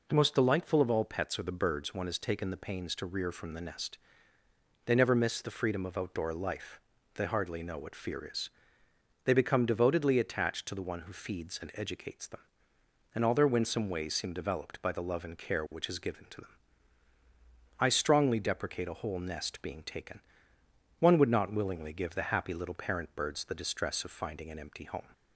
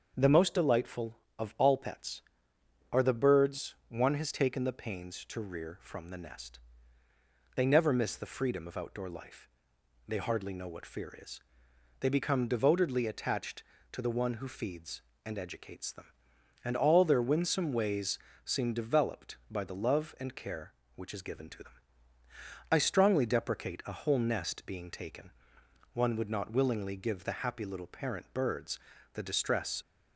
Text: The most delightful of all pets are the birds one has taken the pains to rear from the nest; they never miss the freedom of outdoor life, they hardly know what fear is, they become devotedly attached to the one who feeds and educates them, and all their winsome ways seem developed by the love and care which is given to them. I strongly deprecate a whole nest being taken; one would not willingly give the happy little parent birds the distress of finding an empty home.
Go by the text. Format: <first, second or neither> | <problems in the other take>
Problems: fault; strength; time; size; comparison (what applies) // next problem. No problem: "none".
first | starts louder than the rest; until 1.1 s; 6.5 dB // pauses between "ways" and "seem"; slight; at 18.1 s; 0.28 s long // pauses between "birds" and "the"; at 28.7 s; 0.38 s long // stops before "of finding an empty home"; at 29.8 s